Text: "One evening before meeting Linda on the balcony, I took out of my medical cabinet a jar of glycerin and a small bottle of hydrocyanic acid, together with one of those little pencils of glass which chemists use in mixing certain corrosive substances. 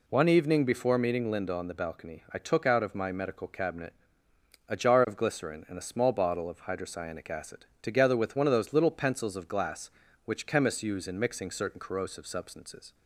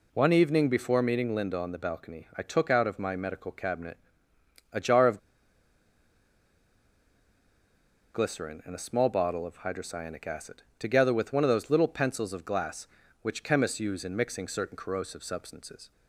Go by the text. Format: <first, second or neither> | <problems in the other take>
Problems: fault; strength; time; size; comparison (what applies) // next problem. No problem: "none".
first | pauses between "cabinet" and "a"; noticeable; at 3.9 s; 0.76 s long; noticeable in the first // pauses between "of" and "glycerin"; strong; at 5.1 s; 2.9 s long